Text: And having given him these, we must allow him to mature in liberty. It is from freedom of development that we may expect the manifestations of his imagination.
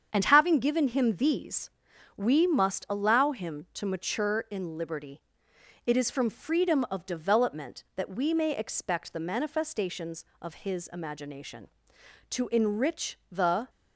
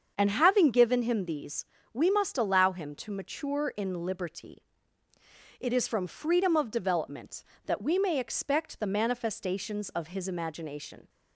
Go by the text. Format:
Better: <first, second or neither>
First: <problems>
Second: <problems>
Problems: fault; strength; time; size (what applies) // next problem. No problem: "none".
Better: second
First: starts louder than the rest; strong; until 1.1 s; 7.5 dB // goes on to say "To enrich the"; from 12.3 s on; 1.3 s long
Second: starts louder than the rest; until 1.1 s; 7 dB